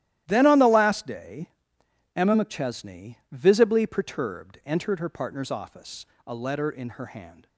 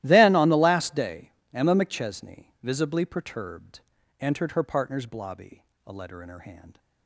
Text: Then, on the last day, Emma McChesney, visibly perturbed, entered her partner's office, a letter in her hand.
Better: first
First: starts louder than the rest; strong; until 1.2 s; 13.5 dB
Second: starts louder than the rest; strong; until 1.0 s; 14.5 dB // says "blobby" for "office"; at 5.0 s

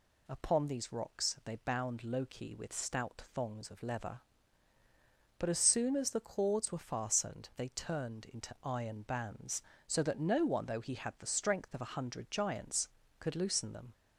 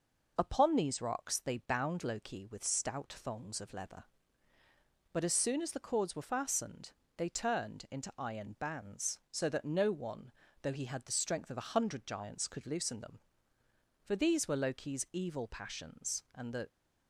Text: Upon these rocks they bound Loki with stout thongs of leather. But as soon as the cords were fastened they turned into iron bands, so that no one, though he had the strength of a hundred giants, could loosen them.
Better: first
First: none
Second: pauses between "fastened" and "they"; slight; at 6.9 s; 0.26 s long // goes on to say "For these were Loki's evil passions and the"; strong; from 14.0 s on; 2.6 s long

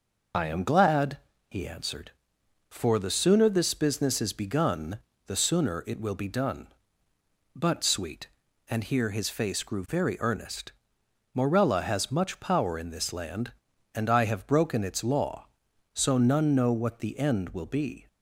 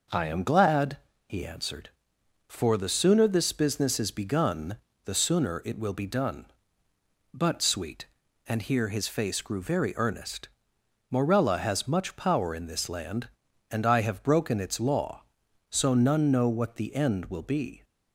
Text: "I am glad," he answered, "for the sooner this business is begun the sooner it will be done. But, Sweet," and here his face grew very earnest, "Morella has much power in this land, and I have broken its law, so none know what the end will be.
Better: second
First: loses the start of "I"; at 0.3 s; 45 ms // pauses between "begun" and "the"; slight; at 4.9 s; 0.26 s long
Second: pauses between "begun" and "the"; slight; at 4.7 s; 0.26 s long

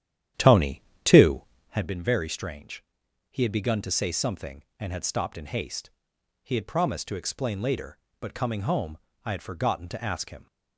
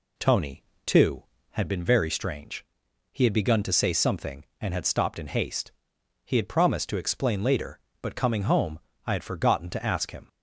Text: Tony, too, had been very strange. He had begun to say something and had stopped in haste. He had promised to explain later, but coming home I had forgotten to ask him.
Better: second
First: starts louder than the rest; strong; until 1.9 s; 10.5 dB // pauses between "home" and "I"; slight; at 8.9 s; 0.26 s long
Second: pauses between "home" and "I"; slight; at 8.7 s; 0.26 s long

